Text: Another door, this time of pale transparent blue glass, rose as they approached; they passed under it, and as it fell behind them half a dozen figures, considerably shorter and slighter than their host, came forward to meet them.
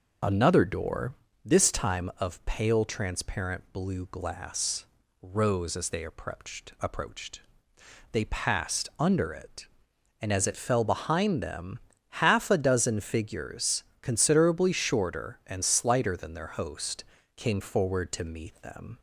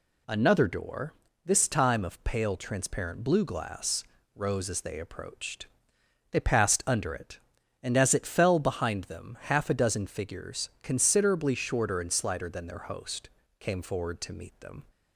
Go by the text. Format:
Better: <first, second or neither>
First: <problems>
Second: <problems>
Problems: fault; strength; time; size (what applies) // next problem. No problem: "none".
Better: second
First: says "approached" twice; at 6.7 s // pauses between "them" and "half"; noticeable; at 11.7 s; 0.46 s long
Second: none